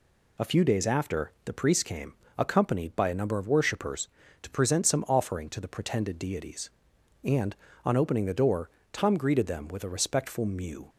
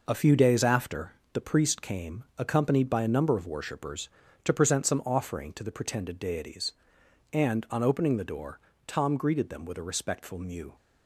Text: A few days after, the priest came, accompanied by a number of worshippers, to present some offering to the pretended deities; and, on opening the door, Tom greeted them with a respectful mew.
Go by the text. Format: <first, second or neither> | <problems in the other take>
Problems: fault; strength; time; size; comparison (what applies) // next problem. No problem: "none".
neither | none